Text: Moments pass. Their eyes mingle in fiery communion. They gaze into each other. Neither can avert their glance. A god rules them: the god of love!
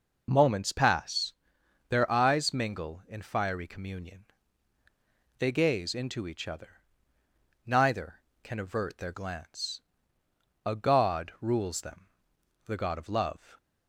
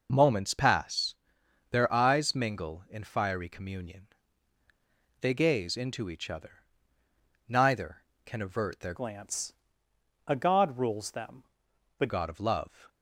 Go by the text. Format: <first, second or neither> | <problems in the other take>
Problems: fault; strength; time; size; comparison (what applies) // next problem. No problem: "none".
first | changes voice from "glance" to "the"; from 8.9 to 12.0 s; 3.1 s long